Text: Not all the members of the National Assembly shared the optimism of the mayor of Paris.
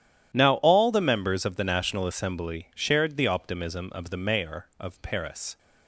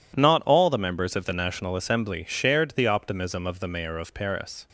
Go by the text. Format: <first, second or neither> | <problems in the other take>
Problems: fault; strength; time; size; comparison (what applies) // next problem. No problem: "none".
second | says "Now" for "Not"; at 0.3 s